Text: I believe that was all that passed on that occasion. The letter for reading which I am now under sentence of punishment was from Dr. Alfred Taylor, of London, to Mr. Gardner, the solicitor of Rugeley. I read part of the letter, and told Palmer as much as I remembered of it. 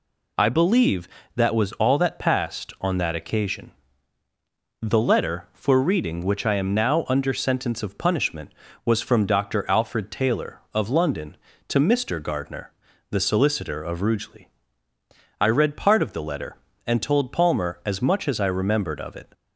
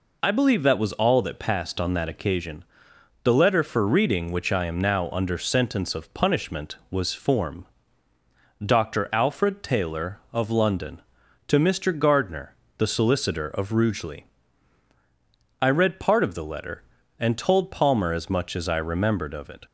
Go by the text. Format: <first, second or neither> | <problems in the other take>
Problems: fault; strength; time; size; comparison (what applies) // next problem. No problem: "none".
first | says "form" for "from"; at 7.1 s